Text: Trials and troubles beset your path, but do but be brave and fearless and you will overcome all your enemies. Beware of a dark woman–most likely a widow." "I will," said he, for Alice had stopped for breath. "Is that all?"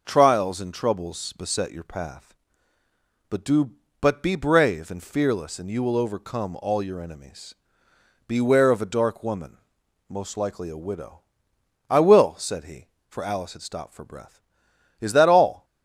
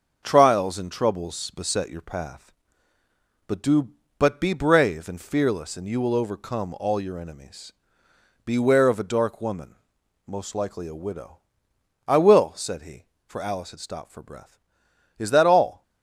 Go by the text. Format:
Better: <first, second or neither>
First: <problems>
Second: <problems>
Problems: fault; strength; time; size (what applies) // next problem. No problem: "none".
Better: first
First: none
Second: gets quieter; noticeable; throughout; 4.5 dB